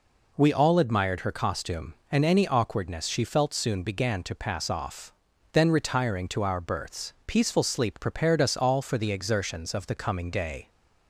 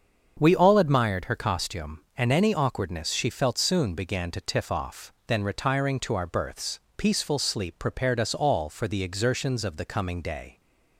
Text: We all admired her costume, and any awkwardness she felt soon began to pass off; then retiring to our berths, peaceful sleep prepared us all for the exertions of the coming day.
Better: first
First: none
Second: starts louder than the rest; until 1.4 s; 7 dB // says "tiff" for "pass"; at 4.3 s

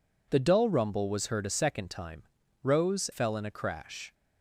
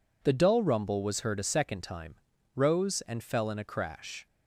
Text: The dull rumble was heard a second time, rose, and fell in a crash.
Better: second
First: skips "and"; at 3.1 s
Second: none

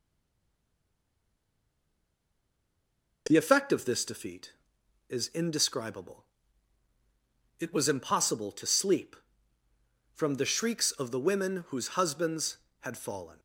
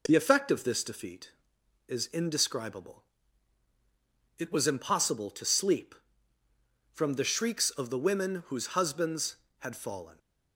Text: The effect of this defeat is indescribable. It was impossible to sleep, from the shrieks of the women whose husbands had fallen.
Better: second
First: stays silent before the first word; strong; until 3.2 s; 3.2 s long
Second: none

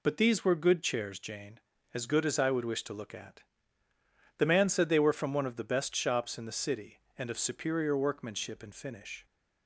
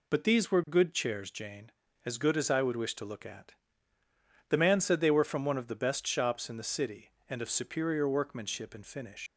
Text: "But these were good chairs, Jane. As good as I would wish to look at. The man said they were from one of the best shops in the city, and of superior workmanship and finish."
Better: first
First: none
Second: leaves "finish" unfinished; at 9.2 s; 100 ms

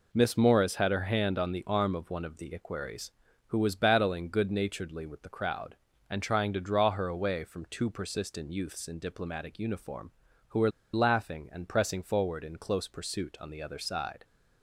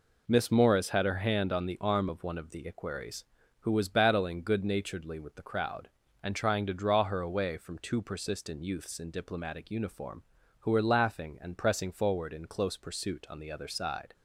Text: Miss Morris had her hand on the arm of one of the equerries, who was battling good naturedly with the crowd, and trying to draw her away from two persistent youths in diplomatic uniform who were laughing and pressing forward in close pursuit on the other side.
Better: second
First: pauses between "were" and "laughing"; slight; at 10.7 s; 0.22 s long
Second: none

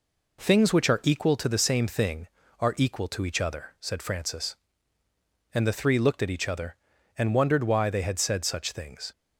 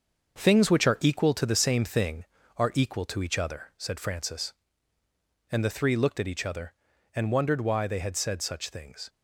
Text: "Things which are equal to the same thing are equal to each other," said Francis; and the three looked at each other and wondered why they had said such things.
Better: first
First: none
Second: gets quieter; throughout; 6.5 dB

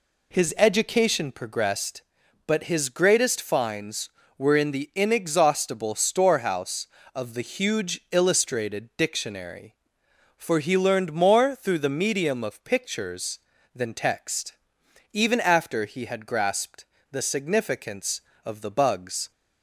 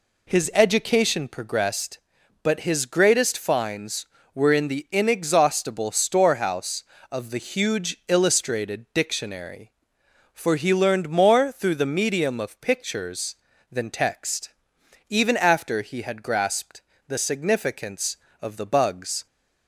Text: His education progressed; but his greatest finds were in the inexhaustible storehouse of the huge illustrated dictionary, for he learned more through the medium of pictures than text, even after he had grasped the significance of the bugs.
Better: neither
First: pauses between "grasped" and "the"; slight; at 16.8 s; 0.26 s long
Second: pauses between "grasped" and "the"; slight; at 16.8 s; 0.26 s long

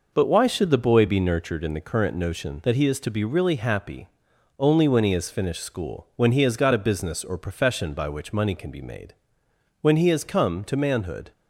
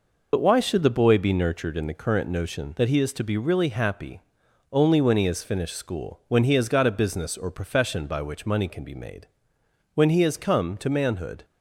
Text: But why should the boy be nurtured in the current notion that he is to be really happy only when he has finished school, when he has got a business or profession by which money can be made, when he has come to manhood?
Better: first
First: pauses between "happy" and "only"; noticeable; at 4.0 s; 0.52 s long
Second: loses the start of "But"; at 0.3 s; 65 ms // pauses between "happy" and "only"; noticeable; at 4.1 s; 0.52 s long

